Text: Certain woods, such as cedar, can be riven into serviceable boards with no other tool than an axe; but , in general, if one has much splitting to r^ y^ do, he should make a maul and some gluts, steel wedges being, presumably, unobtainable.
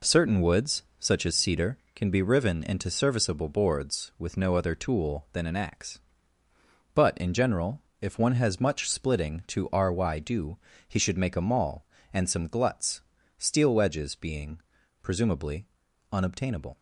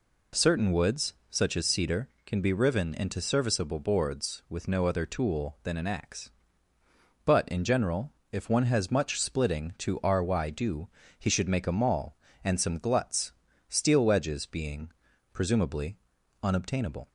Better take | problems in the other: second | gets quieter; strong; throughout; 8.5 dB

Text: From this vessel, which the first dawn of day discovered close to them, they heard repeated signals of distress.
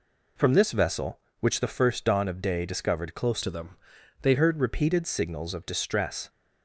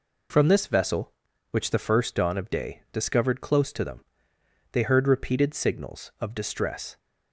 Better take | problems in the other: second | changes voice from "to" to "they"; from 3.4 to 4.3 s; 0.9 s long

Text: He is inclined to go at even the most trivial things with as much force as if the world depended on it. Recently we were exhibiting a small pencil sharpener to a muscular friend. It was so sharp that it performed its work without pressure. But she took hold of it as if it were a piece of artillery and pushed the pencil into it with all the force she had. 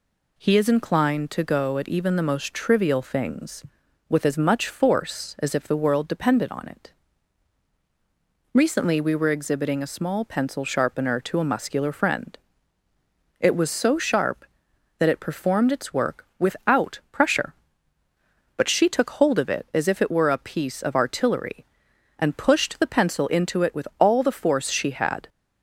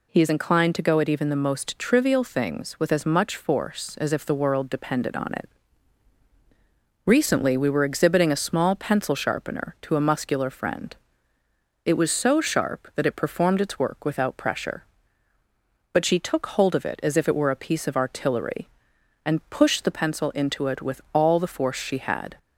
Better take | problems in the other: neither | none

